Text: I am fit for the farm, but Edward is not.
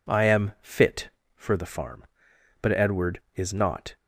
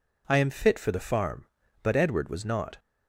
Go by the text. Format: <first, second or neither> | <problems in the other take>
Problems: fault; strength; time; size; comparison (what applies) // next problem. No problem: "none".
first | says "was" for "is"; at 2.2 s